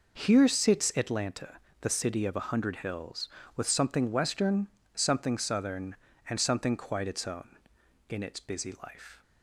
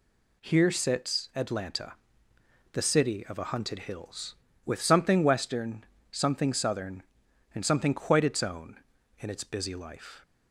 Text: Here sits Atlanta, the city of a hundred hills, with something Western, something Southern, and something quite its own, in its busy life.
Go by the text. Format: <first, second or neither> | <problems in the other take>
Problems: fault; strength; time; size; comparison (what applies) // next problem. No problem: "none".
first | says "hunted" for "hundred"; at 3.4 s